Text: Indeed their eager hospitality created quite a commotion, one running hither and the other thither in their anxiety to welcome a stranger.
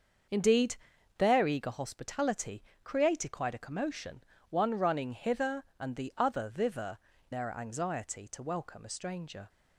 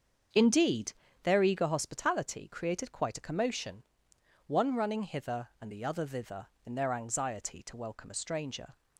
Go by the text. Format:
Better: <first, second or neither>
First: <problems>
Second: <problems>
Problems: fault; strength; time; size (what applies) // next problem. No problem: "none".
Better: second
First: starts louder than the rest; until 1.7 s; 6.5 dB // pauses between "Indeed" and "their"; at 0.7 s; 0.42 s long // pauses between "hospitality" and "created"; slight; at 2.6 s; 0.22 s long // skips "in"; at 7.1 s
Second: starts louder than the rest; strong; until 1.6 s; 7 dB // pauses between "Indeed" and "their"; slight; at 0.9 s; 0.30 s long